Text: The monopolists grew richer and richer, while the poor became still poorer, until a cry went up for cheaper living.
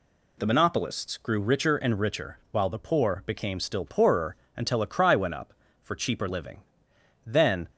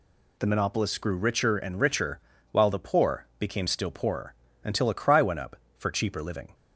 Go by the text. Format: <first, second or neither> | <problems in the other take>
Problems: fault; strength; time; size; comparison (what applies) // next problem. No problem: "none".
second | goes on to say "Then"; slight; from 7.2 s on; 0.42 s long